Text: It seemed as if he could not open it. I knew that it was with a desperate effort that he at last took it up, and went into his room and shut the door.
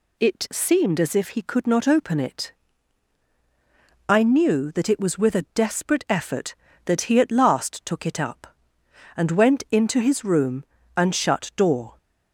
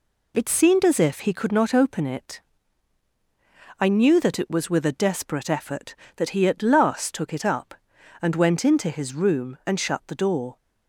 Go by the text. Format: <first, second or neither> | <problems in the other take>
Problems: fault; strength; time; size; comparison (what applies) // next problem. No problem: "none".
second | skips "the"; at 11.5 s